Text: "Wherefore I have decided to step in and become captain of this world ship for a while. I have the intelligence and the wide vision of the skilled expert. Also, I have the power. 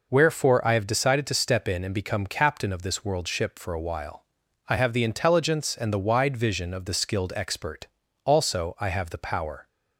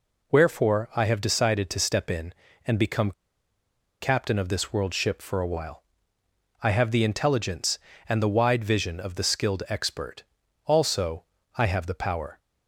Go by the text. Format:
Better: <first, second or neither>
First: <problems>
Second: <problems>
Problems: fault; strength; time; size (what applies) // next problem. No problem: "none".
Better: first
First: none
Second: pauses between "become" and "captain"; noticeable; at 3.1 s; 0.88 s long